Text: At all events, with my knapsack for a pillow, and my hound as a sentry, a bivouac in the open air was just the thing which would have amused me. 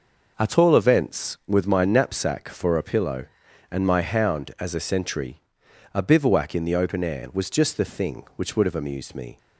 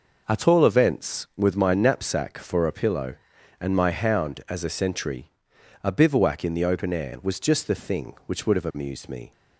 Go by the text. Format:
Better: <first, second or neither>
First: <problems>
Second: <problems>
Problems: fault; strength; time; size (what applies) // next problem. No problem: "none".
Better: neither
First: none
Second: none